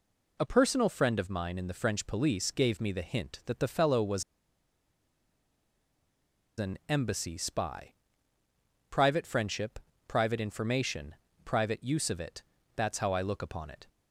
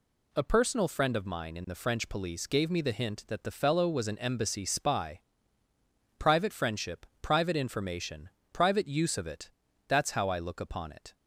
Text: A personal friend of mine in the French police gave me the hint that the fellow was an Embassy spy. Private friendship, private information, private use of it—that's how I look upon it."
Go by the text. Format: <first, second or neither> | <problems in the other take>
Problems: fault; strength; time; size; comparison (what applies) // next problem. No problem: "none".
second | pauses between "was" and "an"; strong; at 4.2 s; 2.3 s long